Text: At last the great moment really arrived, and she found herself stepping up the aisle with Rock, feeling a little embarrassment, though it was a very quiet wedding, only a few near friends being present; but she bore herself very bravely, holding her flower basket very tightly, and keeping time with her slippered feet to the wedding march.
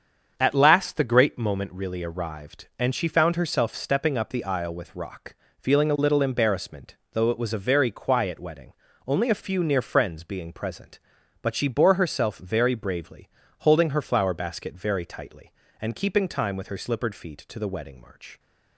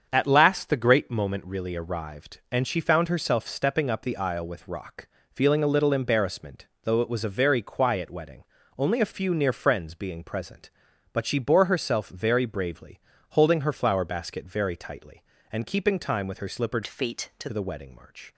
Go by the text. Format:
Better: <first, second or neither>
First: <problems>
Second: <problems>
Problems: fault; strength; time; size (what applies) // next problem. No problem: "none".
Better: first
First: starts louder than the rest; strong; until 1.3 s; 7 dB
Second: starts louder than the rest; strong; until 1.1 s; 7 dB // changes voice from "feet" to "to"; from 16.8 to 17.4 s; 0.6 s long